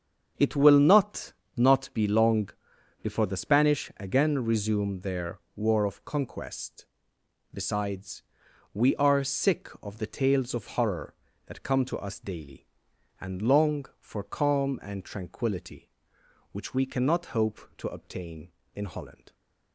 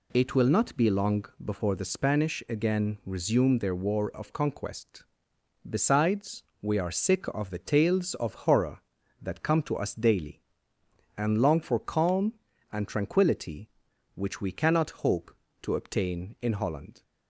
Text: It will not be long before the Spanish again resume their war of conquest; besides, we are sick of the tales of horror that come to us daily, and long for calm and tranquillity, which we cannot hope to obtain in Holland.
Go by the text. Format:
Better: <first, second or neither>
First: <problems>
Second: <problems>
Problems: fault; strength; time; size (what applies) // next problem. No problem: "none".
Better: second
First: starts louder than the rest; strong; until 1.6 s; 7.5 dB // says "not" twice; at 1.5 s // pauses between "long" and "before"; noticeable; at 2.4 s; 0.52 s long // pauses between "their" and "war"; slight; at 5.3 s; 0.16 s long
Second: pauses between "long" and "before"; slight; at 1.2 s; 0.20 s long